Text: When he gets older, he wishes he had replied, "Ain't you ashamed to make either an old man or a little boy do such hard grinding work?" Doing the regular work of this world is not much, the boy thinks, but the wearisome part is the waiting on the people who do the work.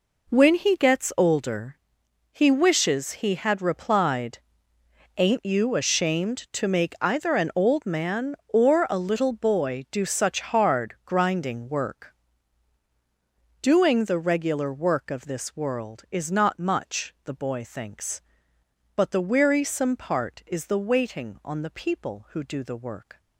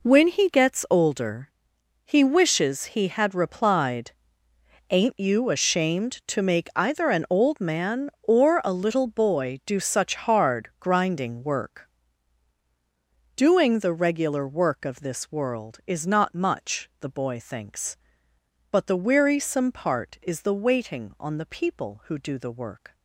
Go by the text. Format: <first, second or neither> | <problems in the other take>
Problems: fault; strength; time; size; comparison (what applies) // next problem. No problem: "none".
neither | none